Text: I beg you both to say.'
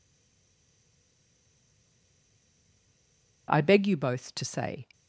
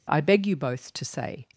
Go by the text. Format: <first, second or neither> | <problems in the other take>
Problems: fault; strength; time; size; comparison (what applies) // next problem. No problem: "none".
second | stays silent before the first word; strong; until 3.4 s; 3.4 s long